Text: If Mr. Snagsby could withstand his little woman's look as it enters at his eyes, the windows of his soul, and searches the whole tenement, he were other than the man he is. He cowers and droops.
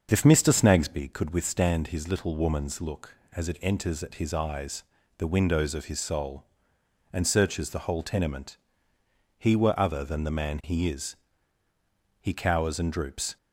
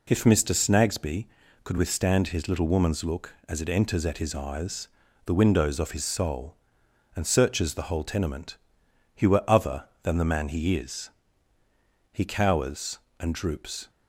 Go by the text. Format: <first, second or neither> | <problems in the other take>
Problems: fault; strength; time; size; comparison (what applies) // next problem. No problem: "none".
second | starts louder than the rest; until 1.1 s; 6.5 dB